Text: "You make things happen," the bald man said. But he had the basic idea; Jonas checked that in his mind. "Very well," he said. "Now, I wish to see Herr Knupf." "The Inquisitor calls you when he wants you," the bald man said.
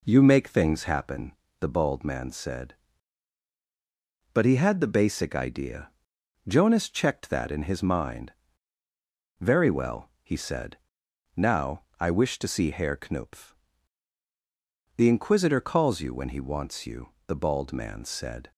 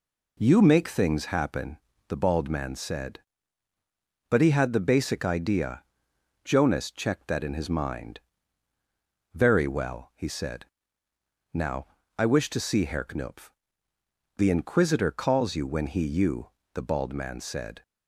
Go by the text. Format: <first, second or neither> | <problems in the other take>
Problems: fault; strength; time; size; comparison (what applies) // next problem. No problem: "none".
first | skips "wants"; at 16.0 s